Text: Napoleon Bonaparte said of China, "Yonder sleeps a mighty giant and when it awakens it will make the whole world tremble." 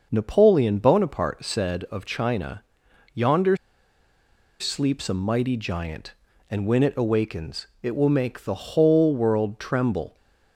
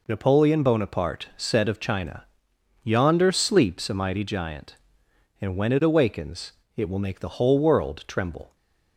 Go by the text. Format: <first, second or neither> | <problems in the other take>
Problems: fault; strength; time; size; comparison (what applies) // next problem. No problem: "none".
second | starts louder than the rest; noticeable; until 1.1 s; 6 dB // pauses between "Yonder" and "sleeps"; at 3.5 s; 1.0 s long // pauses between "awakens" and "it"; slight; at 7.6 s; 0.16 s long; slight in the second